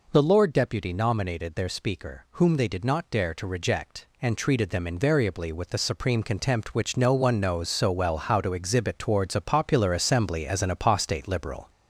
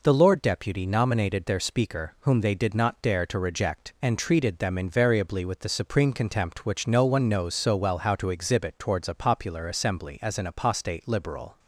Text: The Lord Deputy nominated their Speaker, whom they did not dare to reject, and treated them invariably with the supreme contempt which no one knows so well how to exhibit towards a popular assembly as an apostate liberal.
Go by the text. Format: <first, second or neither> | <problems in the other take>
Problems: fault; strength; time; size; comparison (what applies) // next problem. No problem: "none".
second | gets louder; throughout; 3.5 dB